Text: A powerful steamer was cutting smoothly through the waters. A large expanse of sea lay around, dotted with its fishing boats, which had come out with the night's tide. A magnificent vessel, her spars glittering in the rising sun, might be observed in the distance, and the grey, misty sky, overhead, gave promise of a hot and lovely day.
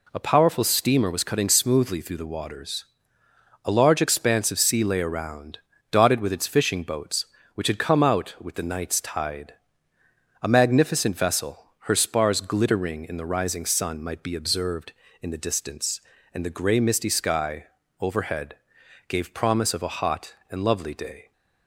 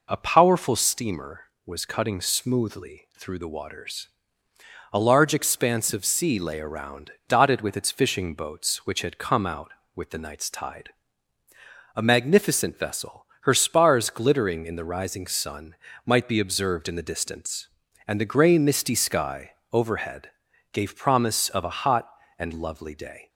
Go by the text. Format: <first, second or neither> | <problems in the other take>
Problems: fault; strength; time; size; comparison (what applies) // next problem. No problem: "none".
neither | none